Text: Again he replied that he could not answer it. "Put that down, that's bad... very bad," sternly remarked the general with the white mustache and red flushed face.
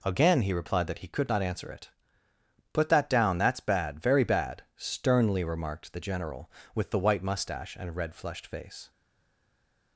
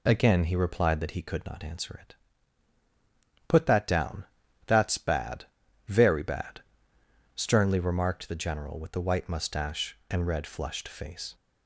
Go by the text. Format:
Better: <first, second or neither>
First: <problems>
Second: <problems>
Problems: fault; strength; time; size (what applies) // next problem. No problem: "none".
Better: second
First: stays silent after the last word; from 8.8 s on; 1.1 s long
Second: none